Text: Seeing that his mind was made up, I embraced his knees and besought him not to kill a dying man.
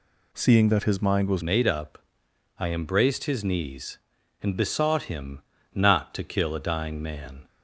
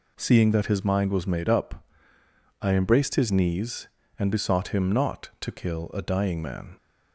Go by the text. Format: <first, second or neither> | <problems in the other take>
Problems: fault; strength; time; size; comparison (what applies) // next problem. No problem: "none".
second | changes voice at "made"; from 1.4 s on; 6.0 s long // pauses between "him" and "not"; slight; at 5.4 s; 0.32 s long